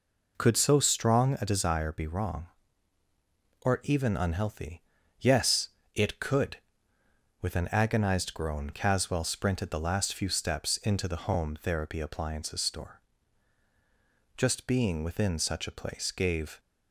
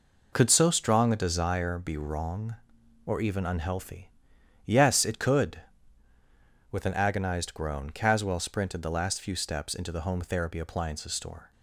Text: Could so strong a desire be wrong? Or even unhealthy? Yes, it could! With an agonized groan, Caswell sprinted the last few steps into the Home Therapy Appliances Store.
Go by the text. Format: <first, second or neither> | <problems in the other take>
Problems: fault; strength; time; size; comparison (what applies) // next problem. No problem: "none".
second | goes on to say "Just being within such a place gave"; strong; from 14.3 s on; 2.2 s long